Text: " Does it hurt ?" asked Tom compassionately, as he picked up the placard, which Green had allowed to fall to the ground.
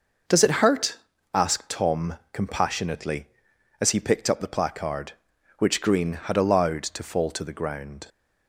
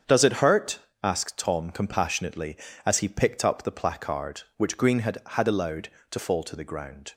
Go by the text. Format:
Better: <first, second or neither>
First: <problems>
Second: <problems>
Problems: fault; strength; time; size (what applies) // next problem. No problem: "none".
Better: first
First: none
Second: starts louder than the rest; until 1.2 s; 7 dB // says "had" twice; at 5.2 s